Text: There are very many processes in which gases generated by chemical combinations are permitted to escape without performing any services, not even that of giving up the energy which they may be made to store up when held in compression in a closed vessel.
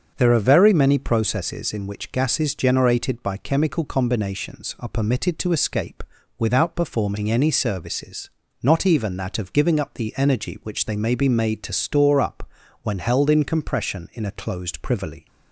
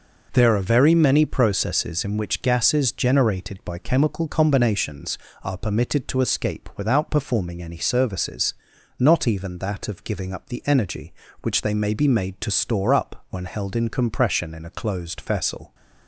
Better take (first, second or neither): second